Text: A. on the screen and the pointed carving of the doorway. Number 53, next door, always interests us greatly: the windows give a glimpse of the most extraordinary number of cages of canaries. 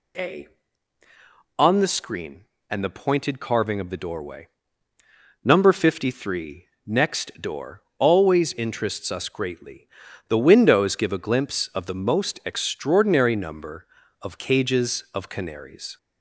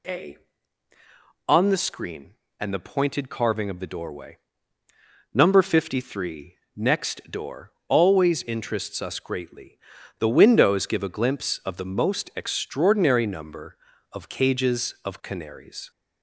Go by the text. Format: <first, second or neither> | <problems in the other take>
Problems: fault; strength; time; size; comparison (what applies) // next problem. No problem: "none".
neither | none